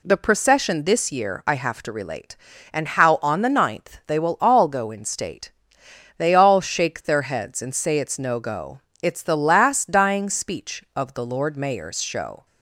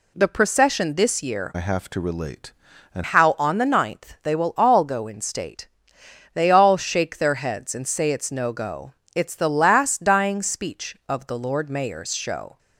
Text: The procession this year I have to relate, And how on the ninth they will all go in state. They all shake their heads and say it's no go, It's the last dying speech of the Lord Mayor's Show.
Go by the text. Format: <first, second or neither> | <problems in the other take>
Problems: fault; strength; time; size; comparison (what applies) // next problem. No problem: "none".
first | changes voice from "I" to "And"; from 1.5 to 3.0 s; 1.5 s long